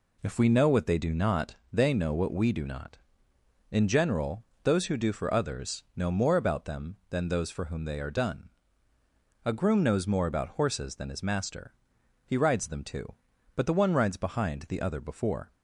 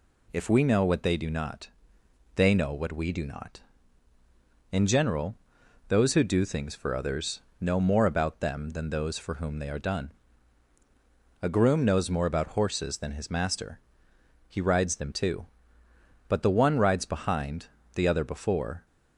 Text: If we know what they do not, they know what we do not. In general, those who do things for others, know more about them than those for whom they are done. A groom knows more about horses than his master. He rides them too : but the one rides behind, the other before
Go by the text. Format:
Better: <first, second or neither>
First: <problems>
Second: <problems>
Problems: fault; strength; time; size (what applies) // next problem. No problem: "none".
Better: second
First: skips "things"; at 5.1 s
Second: none